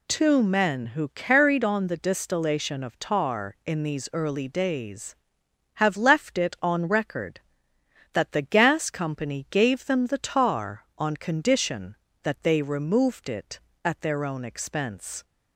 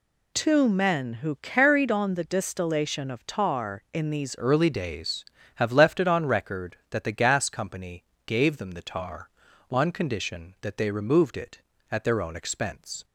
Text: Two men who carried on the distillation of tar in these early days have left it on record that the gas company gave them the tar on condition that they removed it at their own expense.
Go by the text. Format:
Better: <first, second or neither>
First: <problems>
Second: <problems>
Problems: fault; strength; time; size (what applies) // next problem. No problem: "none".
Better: first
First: none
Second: changes voice at "early"; from 4.3 s on; 8.7 s long // pauses between "company" and "gave"; slight; at 8.0 s; 0.22 s long